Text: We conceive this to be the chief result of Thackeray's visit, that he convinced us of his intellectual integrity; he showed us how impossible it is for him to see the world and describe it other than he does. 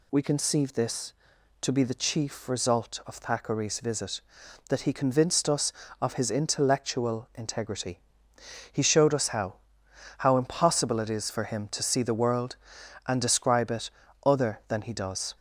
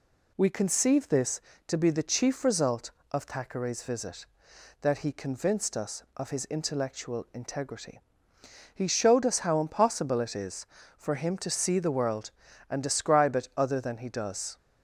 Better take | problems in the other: second | says "how" twice; at 10.1 s // pauses between "it" and "other"; slight; at 13.8 s; 0.36 s long

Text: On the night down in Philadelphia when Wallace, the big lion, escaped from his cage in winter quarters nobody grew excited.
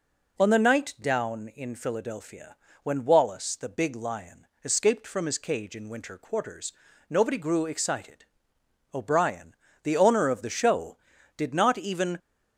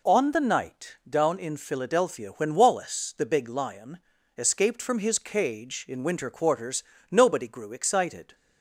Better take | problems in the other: second | pauses between "Philadelphia" and "when"; slight; at 2.5 s; 0.26 s long // pauses between "quarters" and "nobody"; slight; at 6.7 s; 0.34 s long; slight in the second // goes on to say "O'Brien the owner of the show did not even"; strong; from 8.9 s on; 3.2 s long

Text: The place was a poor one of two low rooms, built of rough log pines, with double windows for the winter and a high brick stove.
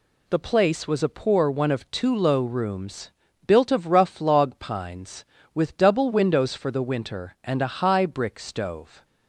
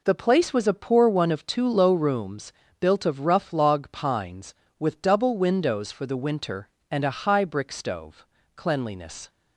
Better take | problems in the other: first | goes on to say "Cleanliness"; noticeable; from 8.5 s on; 0.74 s long

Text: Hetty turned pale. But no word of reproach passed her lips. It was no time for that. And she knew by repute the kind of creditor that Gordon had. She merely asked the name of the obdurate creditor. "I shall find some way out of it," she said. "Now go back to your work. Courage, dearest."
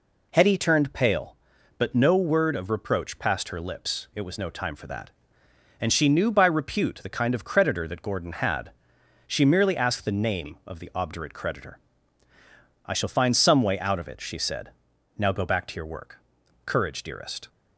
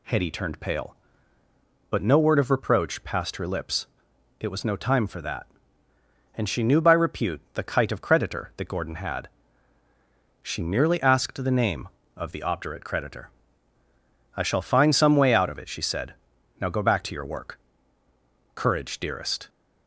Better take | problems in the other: first | says "kite" for "kind"; at 7.6 s

